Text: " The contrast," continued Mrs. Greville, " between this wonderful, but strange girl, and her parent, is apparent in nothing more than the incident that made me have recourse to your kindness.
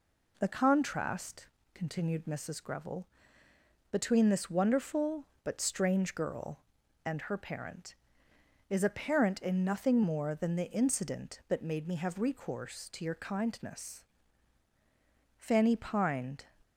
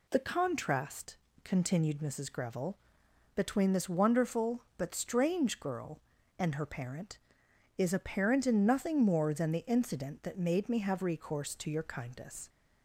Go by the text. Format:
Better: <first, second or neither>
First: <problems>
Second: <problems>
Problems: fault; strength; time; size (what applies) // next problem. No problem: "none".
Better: second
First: goes on to say "Fanny pined"; noticeable; from 15.3 s on; 1.0 s long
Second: none